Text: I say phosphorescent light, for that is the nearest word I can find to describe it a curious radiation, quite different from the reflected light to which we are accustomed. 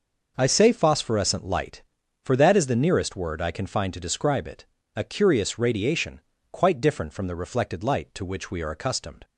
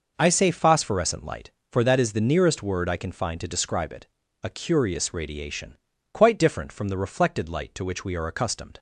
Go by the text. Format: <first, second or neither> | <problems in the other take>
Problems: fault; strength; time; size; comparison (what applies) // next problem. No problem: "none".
neither | pauses between "it" and "a"; the same in both